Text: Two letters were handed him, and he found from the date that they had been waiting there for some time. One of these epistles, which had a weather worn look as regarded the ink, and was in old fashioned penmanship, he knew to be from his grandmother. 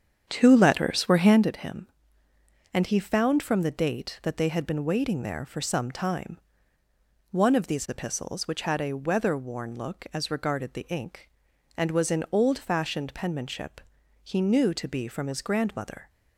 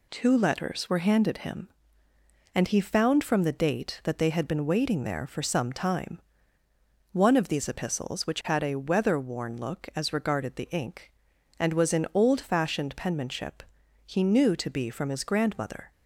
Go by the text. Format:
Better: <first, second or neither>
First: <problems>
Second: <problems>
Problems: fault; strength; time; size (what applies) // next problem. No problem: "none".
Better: second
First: starts louder than the rest; strong; until 1.5 s; 8 dB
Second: none